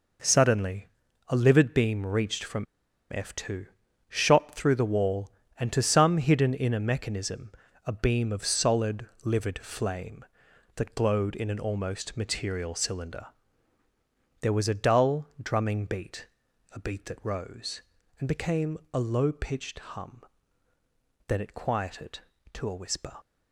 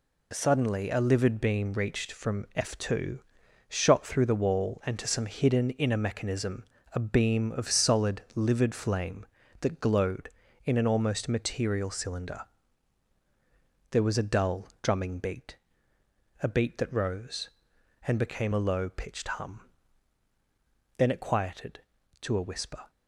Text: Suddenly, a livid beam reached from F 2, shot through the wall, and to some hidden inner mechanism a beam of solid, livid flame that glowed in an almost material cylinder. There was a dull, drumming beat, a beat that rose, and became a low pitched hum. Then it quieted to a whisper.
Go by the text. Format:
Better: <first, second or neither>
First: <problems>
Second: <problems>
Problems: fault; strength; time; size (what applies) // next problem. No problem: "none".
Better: second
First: pauses between "from" and "F"; noticeable; at 2.6 s; 0.48 s long // pauses between "mechanism" and "a"; slight; at 7.5 s; 0.34 s long // pauses between "became" and "a"; slight; at 18.7 s; 0.16 s long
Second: pauses between "mechanism" and "a"; slight; at 6.6 s; 0.30 s long